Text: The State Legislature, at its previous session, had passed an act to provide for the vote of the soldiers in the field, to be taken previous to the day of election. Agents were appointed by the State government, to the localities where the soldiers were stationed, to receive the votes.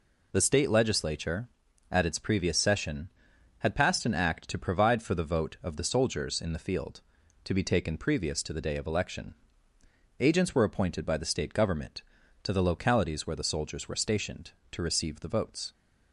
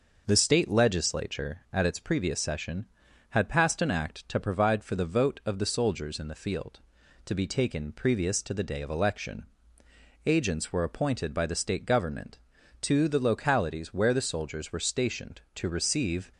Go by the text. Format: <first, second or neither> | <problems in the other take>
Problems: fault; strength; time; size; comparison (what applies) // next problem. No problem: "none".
first | stops before "the votes"; at 16.3 s